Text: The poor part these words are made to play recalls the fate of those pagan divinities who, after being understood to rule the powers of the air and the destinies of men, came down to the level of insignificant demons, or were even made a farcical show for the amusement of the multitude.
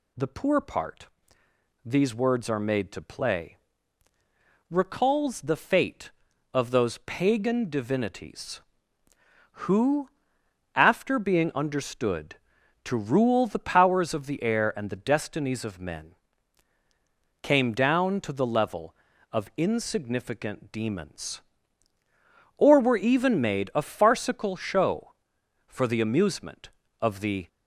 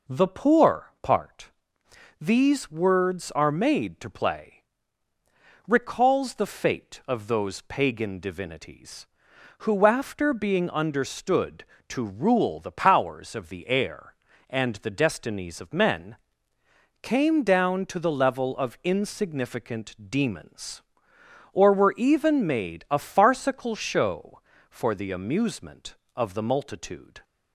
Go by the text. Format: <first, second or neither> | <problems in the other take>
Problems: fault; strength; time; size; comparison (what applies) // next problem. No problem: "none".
second | pauses between "part" and "these"; noticeable; at 1.0 s; 0.78 s long; noticeable in the second // pauses between "play" and "recalls"; at 3.5 s; 1.1 s long; also in the second // stops before "multitude"; at 27.4 s